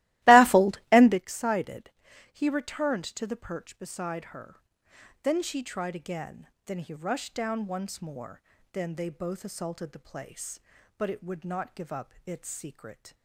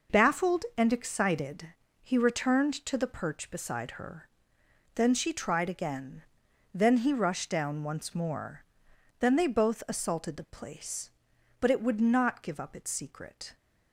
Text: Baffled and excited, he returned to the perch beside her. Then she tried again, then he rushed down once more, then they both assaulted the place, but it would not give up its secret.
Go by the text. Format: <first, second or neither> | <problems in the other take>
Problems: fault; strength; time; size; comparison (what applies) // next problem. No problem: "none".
second | starts louder than the rest; strong; until 1.2 s; 17.5 dB